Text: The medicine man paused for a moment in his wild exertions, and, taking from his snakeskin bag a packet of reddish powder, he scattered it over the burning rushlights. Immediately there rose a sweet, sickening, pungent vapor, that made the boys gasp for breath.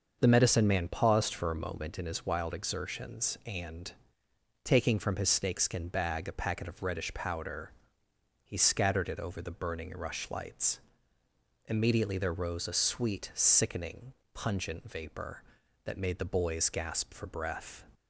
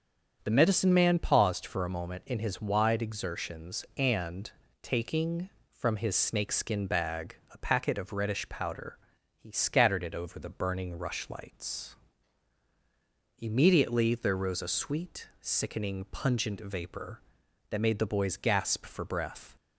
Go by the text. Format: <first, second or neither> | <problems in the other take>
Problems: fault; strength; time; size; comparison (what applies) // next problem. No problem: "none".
first | starts louder than the rest; strong; until 1.4 s; 7.5 dB; also in the first // says "wide" for "wild"; at 2.6 s // pauses between "bag" and "a"; slight; at 7.3 s; 0.16 s long